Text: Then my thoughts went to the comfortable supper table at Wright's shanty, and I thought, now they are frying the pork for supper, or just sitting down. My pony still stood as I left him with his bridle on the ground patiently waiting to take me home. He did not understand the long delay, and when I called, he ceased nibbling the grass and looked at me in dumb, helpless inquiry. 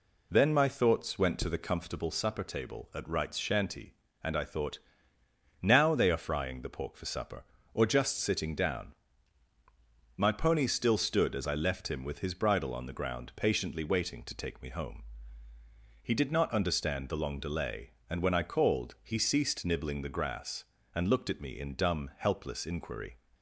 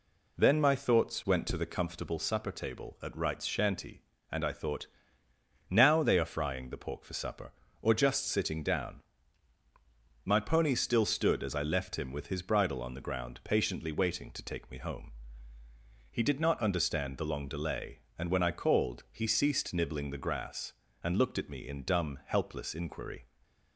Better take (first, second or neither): neither